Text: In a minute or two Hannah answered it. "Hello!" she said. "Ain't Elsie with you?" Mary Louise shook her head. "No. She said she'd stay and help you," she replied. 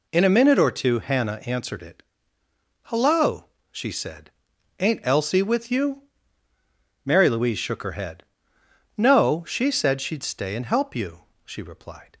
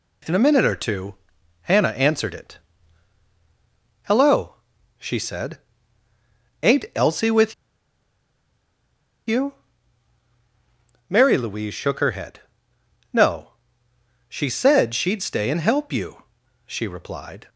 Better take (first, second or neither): first